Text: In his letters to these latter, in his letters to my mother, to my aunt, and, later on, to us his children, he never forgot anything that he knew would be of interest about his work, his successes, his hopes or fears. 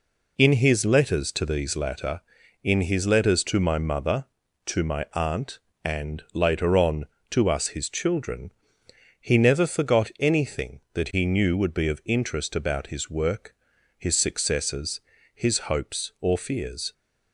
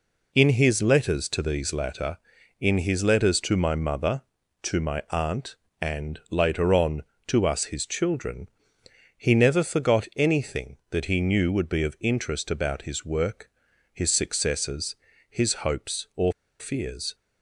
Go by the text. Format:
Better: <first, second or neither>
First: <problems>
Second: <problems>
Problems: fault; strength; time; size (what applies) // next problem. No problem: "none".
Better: first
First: none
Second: pauses between "or" and "fears"; slight; at 16.3 s; 0.27 s long